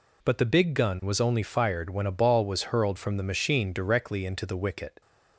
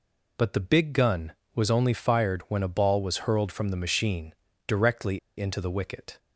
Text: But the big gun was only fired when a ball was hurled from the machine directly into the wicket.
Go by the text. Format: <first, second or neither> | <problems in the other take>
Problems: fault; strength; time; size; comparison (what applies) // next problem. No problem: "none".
first | pauses between "machine" and "directly"; slight; at 4.3 s; 0.32 s long // pauses between "directly" and "into"; slight; at 5.1 s; 0.20 s long